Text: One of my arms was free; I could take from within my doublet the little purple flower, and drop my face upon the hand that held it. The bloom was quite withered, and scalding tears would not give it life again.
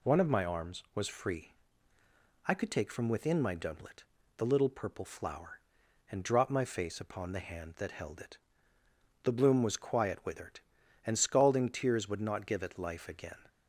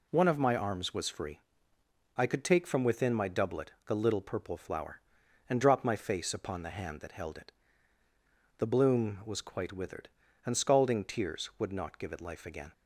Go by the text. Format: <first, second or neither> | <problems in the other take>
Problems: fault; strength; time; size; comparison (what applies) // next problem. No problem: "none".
second | pauses between "doublet" and "the"; slight; at 4.0 s; 0.36 s long; slight in the second // says "quiet" for "quite"; at 9.7 s